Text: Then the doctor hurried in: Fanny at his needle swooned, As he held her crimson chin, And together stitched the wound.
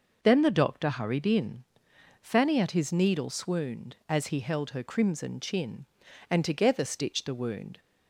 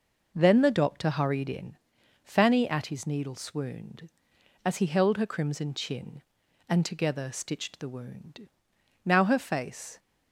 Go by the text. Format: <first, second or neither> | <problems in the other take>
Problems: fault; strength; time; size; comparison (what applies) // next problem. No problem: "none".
first | goes on to say "Now her face"; noticeable; from 9.0 s on; 0.94 s long